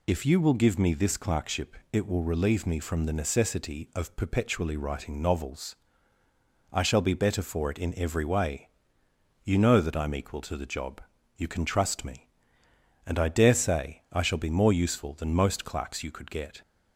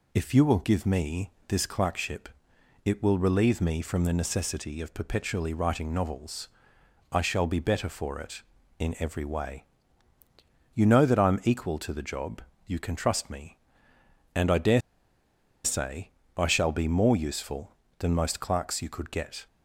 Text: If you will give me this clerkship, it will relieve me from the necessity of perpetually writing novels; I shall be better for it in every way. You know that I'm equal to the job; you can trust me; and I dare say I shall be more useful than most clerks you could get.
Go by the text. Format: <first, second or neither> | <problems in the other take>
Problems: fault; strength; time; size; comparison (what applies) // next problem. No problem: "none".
first | pauses between "me" and "this"; slight; at 1.3 s; 0.16 s long // pauses between "dare" and "say"; noticeable; at 14.8 s; 0.83 s long // pauses between "say" and "I"; slight; at 16.1 s; 0.26 s long